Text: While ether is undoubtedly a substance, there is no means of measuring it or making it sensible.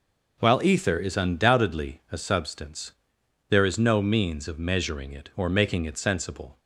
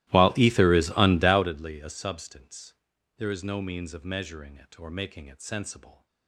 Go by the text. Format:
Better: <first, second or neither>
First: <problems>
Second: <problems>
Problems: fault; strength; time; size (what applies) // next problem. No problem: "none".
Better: first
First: none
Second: starts louder than the rest; strong; until 1.6 s; 16.5 dB